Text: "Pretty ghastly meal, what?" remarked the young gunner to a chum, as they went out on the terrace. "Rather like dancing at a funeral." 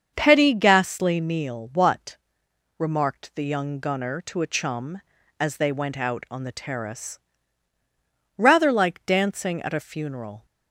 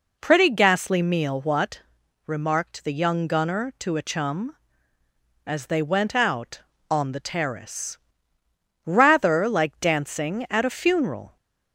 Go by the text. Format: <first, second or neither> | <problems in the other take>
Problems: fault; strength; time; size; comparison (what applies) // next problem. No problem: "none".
second | starts louder than the rest; until 1.1 s; 7 dB // says "Petty" for "Pretty"; at 0.1 s